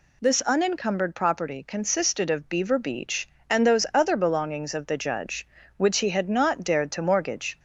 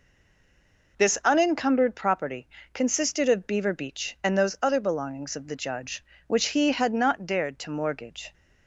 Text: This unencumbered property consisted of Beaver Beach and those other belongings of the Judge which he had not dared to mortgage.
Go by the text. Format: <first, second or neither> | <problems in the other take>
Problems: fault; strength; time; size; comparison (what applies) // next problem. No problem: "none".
first | stays silent before the first word; until 0.9 s; 0.9 s long // pauses between "property" and "consisted"; slight; at 2.4 s; 0.26 s long